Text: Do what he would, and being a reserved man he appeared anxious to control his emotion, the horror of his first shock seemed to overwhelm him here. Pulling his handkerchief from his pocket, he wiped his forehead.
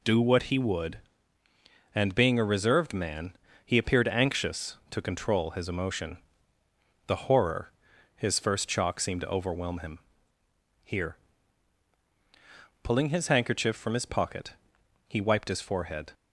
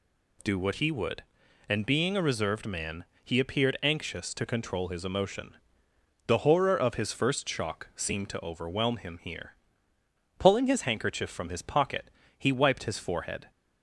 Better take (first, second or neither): second